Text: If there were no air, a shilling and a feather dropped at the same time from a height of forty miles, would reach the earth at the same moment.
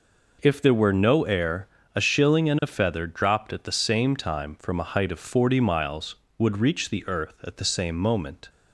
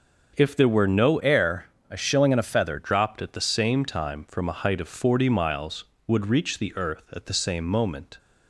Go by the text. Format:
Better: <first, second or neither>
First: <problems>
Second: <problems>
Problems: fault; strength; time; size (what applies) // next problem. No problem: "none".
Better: first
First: none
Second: starts louder than the rest; until 1.3 s; 6.5 dB // changes voice from "air" to "feather"; from 1.1 to 2.7 s; 1.6 s long